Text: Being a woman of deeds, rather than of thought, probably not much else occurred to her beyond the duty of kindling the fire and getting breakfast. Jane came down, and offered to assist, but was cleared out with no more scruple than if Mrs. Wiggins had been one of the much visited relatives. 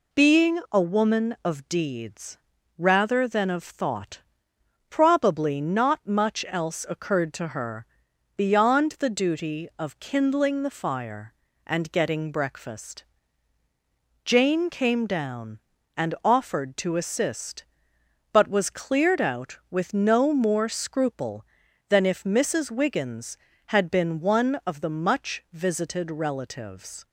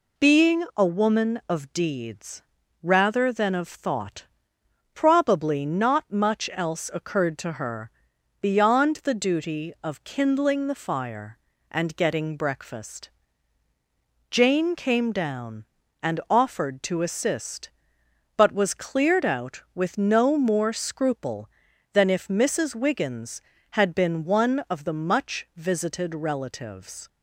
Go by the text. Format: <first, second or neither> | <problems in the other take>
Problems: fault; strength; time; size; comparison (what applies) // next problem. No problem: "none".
neither | pauses between "her" and "beyond"; noticeable; the same in both